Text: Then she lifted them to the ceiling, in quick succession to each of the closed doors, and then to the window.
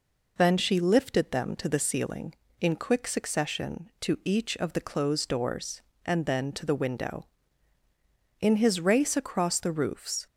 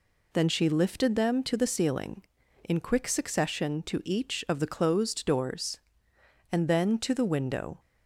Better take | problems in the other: second | goes on to say "In his race across the roofs"; strong; from 8.3 s on; 1.8 s long

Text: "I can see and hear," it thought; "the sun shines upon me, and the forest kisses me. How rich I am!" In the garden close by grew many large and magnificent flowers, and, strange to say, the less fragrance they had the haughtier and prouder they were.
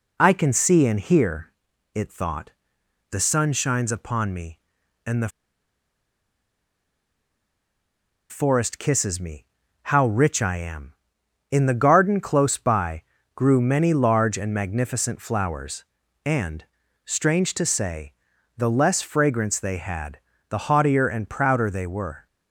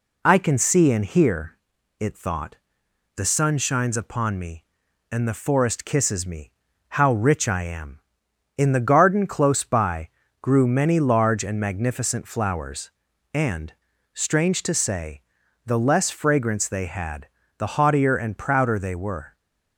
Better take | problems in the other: second | pauses between "the" and "forest"; strong; at 5.2 s; 3.0 s long // pauses between "by" and "grew"; slight; at 13.0 s; 0.30 s long; slight in the second // pauses between "had" and "the"; slight; at 20.1 s; 0.30 s long; slight in the second

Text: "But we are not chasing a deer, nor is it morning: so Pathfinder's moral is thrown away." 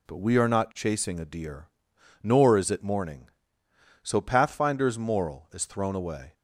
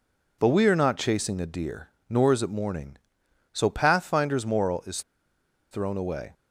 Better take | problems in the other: first | pauses between "is" and "thrown"; noticeable; at 5.0 s; 0.69 s long

